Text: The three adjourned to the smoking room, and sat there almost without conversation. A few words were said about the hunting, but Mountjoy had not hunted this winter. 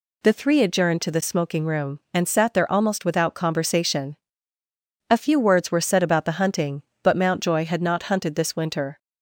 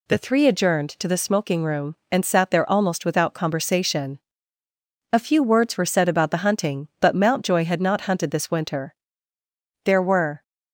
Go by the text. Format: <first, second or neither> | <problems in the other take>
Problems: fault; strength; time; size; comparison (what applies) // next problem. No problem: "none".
first | goes on to say "There were"; from 9.8 s on; 0.58 s long